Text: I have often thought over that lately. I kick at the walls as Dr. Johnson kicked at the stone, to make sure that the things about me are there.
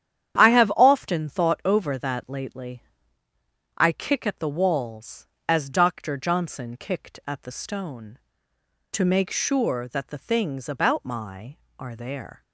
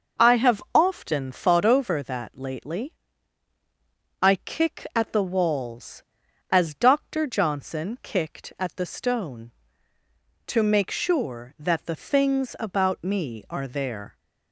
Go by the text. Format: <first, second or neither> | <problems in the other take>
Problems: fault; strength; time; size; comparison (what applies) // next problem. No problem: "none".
second | starts louder than the rest; strong; until 1.4 s; 9.5 dB // says "my" for "me"; at 11.0 s